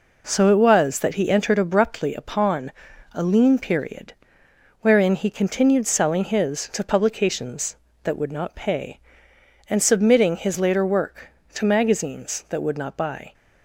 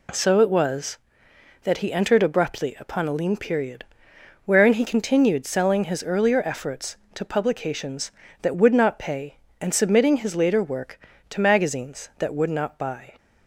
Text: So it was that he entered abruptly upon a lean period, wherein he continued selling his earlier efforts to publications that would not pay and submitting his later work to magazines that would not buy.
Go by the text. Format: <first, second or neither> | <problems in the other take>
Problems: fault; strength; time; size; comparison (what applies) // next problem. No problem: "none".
second | pauses between "upon" and "a"; at 2.7 s; 0.42 s long // skips "earlier efforts"; at 6.6 s